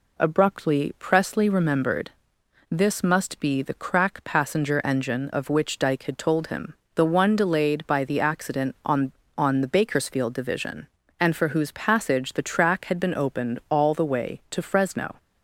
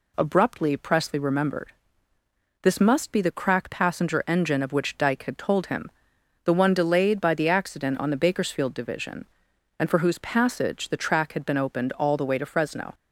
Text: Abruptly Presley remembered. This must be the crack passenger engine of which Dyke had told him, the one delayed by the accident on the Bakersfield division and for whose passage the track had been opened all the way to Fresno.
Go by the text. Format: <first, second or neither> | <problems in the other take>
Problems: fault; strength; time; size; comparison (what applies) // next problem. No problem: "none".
second | says "on" twice; at 9.3 s